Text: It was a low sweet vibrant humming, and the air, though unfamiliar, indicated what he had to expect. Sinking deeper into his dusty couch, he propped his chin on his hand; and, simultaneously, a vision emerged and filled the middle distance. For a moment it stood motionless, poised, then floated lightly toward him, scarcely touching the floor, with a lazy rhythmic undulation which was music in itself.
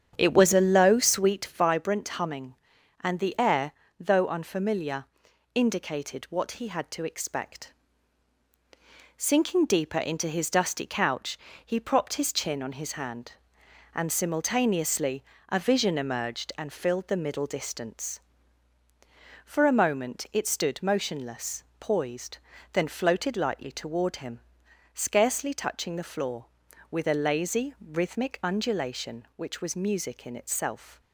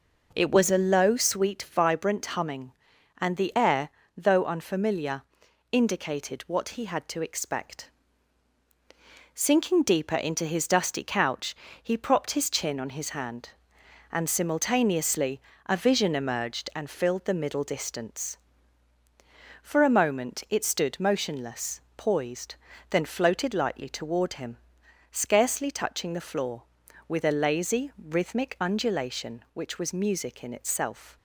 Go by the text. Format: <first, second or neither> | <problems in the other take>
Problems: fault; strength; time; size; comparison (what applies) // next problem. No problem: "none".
second | starts louder than the rest; strong; until 1.7 s; 8.5 dB